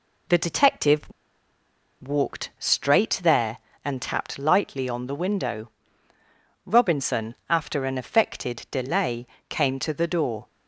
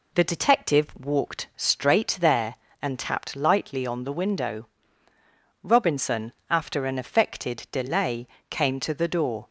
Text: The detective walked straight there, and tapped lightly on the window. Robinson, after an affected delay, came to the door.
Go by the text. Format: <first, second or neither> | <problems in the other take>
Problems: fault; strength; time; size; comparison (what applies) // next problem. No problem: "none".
second | pauses between "detective" and "walked"; at 1.0 s; 0.98 s long